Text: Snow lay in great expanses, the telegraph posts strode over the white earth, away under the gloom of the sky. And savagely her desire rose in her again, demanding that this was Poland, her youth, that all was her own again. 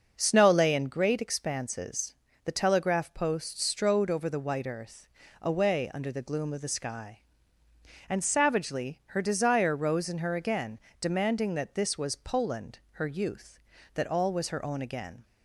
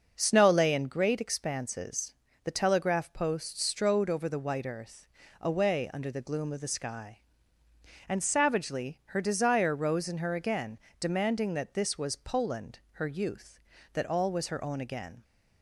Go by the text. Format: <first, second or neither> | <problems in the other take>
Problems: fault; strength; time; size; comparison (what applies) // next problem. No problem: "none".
neither | starts louder than the rest; the same in both